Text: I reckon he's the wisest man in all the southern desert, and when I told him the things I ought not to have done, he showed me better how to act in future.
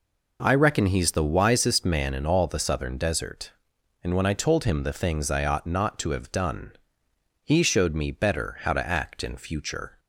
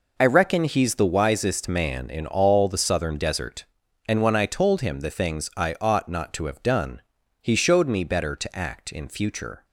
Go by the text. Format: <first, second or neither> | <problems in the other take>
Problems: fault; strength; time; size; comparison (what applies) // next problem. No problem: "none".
first | skips "how"; at 8.3 s